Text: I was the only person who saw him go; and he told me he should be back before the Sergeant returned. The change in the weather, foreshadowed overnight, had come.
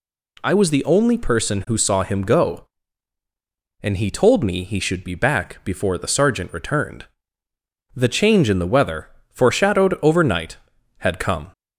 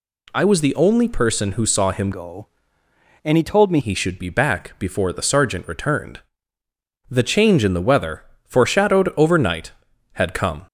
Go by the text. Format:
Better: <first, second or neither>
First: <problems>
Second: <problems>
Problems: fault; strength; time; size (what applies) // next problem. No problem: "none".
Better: first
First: none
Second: changes voice from "go" to "me"; from 2.1 to 3.7 s; 1.6 s long